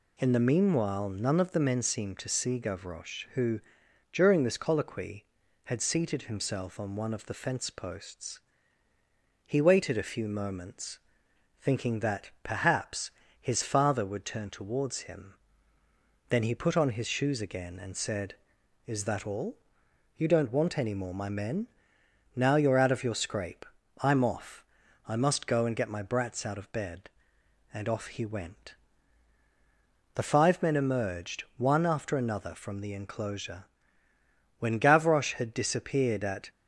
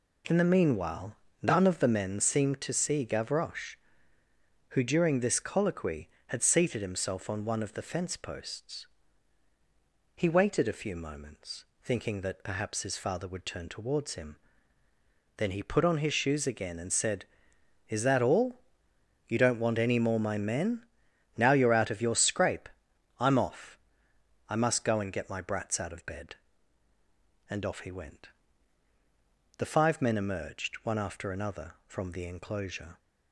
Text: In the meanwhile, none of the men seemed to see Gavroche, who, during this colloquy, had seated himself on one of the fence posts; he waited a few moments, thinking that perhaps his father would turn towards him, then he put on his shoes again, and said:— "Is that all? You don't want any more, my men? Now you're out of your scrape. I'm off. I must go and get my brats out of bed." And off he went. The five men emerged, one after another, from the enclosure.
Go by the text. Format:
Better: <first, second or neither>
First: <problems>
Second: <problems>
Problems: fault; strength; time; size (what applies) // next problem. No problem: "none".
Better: second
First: pauses between "perhaps" and "his"; slight; at 13.1 s; 0.30 s long // goes on to say "When Gavroche had disappeared at"; strong; from 34.5 s on; 1.9 s long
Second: none